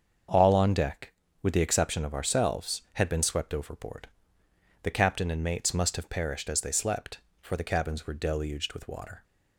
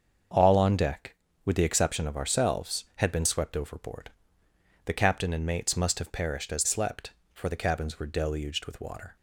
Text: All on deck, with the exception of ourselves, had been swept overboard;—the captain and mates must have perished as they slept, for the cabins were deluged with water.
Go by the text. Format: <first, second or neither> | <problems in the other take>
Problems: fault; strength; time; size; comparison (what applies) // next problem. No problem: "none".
first | starts louder than the rest; until 1.6 s; 7 dB; also in the first // skips "they"; at 6.6 s